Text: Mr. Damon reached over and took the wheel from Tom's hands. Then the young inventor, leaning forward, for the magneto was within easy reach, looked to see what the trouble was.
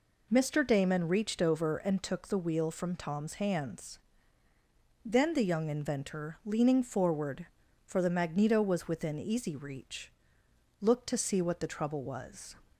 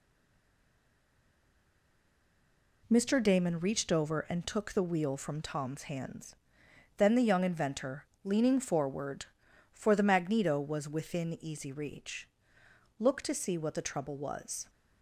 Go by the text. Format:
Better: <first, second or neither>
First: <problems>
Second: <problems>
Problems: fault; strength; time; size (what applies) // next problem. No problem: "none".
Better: first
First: none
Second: stays silent before the first word; strong; until 2.8 s; 2.8 s long